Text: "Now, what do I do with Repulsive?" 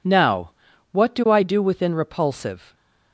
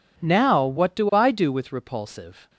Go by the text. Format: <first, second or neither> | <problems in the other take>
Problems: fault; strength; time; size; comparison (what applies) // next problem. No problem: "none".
second | says "within" for "with"; at 1.6 s